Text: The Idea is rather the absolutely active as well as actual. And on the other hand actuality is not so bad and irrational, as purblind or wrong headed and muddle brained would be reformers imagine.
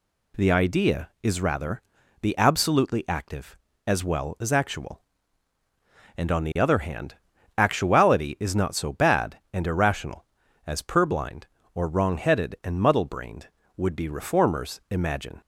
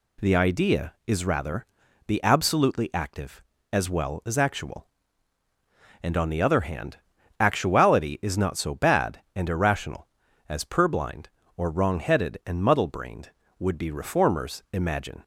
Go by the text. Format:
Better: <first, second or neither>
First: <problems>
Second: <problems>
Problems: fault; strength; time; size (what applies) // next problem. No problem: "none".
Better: neither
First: pauses between "rather" and "the"; at 1.8 s; 0.40 s long // pauses between "hand" and "actuality"; at 7.1 s; 0.42 s long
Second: pauses between "rather" and "the"; at 1.6 s; 0.41 s long // pauses between "hand" and "actuality"; at 6.9 s; 0.42 s long